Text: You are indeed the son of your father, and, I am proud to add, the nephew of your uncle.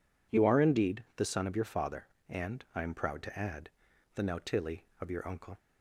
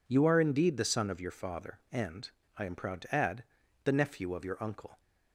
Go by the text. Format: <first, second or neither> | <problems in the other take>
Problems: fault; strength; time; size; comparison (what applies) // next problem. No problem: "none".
second | says "nautili" for "nephew"; at 4.2 s